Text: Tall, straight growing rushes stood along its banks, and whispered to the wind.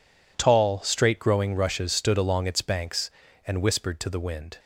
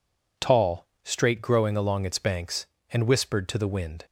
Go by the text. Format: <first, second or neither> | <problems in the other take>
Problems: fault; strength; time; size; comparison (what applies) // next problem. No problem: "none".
first | skips "rushes stood"; at 1.7 s